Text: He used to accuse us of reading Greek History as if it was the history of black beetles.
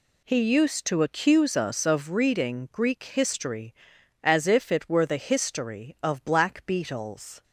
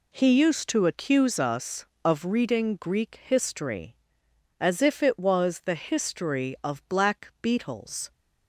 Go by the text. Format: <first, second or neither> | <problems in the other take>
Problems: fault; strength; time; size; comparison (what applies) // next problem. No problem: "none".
second | says "were" for "was"; at 4.8 s